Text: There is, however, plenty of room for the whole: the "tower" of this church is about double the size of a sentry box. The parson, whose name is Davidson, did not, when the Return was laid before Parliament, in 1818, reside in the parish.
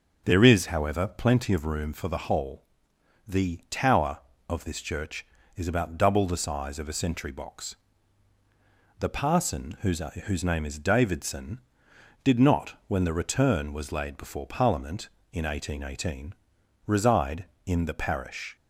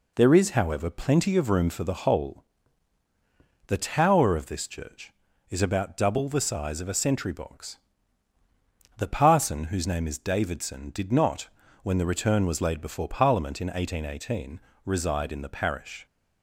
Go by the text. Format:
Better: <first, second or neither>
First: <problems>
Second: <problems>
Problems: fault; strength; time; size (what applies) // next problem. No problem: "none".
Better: second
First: says "whose" twice; at 10.2 s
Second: none